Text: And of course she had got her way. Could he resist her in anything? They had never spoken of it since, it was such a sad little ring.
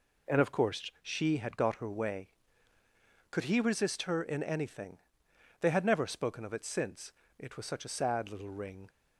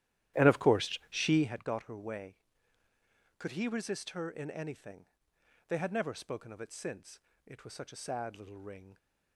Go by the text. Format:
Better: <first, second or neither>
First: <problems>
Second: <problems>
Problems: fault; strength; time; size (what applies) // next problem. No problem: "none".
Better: first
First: none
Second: starts louder than the rest; strong; until 1.6 s; 13 dB